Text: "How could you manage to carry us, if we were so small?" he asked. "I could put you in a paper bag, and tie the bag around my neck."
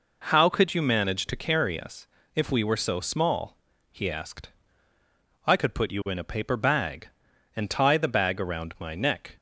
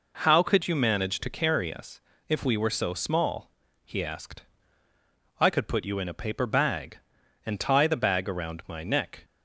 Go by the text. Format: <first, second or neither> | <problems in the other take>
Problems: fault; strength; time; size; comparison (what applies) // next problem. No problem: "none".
neither | none